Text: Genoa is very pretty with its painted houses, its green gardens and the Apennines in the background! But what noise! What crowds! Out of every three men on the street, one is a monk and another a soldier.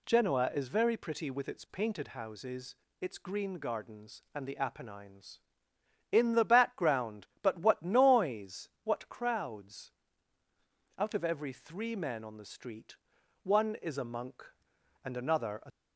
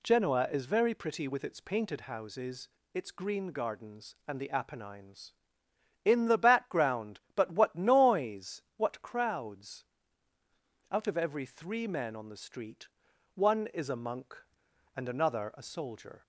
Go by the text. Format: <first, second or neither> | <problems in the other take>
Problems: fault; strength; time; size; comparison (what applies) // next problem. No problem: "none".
second | stops before "soldier"; at 15.7 s